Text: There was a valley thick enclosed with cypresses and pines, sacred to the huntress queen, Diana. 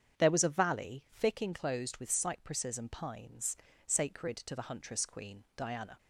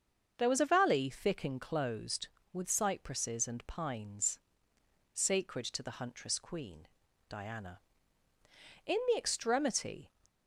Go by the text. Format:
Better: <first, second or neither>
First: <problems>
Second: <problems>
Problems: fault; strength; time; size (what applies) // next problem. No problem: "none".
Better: first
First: starts louder than the rest; strong; until 1.2 s; 8 dB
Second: starts louder than the rest; until 1.3 s; 6.5 dB // goes on to say "In the extremity"; noticeable; from 8.8 s on; 1.2 s long